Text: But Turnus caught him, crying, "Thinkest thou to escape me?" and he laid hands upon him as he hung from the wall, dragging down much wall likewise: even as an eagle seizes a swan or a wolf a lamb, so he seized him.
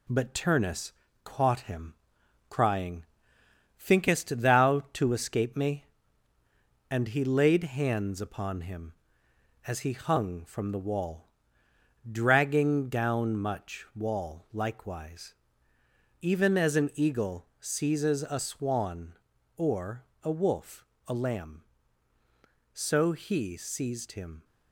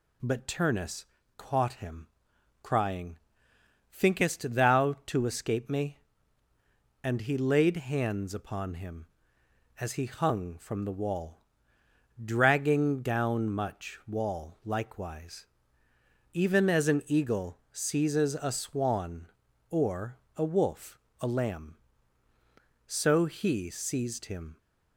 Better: second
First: gets quieter; throughout; 3.5 dB // pauses between "Turnus" and "caught"; slight; at 0.9 s; 0.30 s long // pauses between "or" and "a"; slight; at 20.0 s; 0.18 s long // pauses between "wolf" and "a"; slight; at 20.8 s; 0.24 s long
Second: pauses between "Turnus" and "caught"; slight; at 1.0 s; 0.30 s long // pauses between "or" and "a"; slight; at 20.1 s; 0.18 s long // pauses between "wolf" and "a"; slight; at 20.9 s; 0.24 s long

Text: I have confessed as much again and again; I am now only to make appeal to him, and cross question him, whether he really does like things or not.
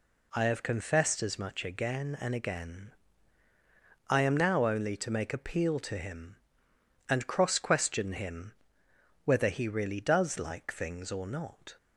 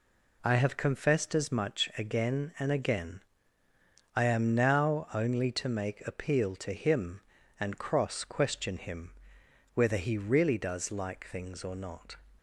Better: neither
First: none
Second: none

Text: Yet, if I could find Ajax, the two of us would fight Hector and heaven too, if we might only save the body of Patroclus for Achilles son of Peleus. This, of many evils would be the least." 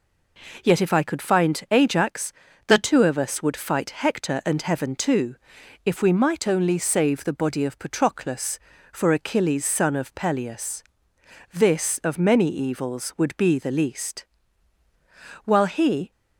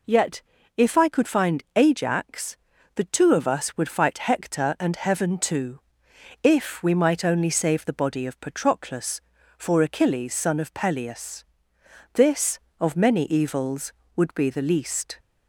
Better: second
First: goes on to say "While he"; noticeable; from 15.4 s on; 0.66 s long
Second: none

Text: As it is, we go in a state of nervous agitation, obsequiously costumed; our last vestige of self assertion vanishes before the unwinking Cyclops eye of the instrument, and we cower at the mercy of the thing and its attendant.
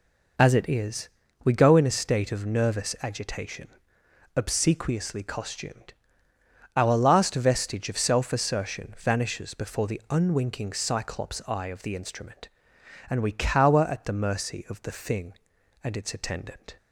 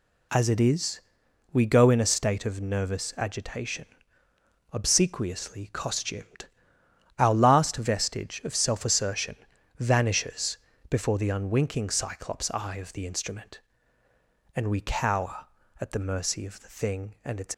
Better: first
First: none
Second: pauses between "assertion" and "vanishes"; at 9.3 s; 0.42 s long // pauses between "vanishes" and "before"; slight; at 10.5 s; 0.32 s long // stops before "attendant"; at 17.5 s

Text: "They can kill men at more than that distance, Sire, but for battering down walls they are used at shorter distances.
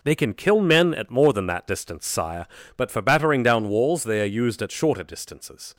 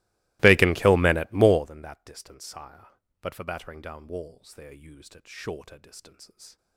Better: first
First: none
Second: starts louder than the rest; strong; until 1.7 s; 22.5 dB

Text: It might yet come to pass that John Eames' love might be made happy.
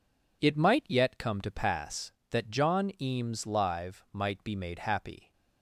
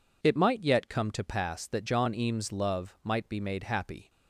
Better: second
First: says "live" for "love"; at 3.4 s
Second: none

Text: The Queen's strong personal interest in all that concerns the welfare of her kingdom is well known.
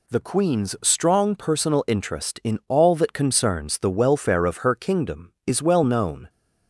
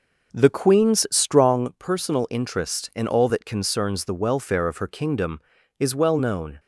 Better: first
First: none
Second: starts louder than the rest; noticeable; until 1.7 s; 5 dB

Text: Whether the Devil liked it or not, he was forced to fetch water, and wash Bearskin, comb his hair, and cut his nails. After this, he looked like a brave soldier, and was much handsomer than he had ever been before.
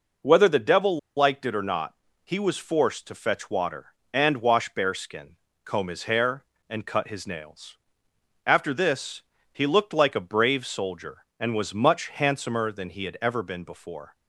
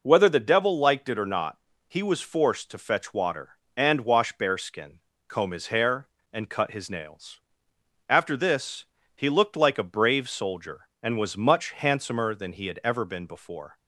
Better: second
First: pauses between "Devil" and "liked"; slight; at 0.9 s; 0.18 s long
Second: none

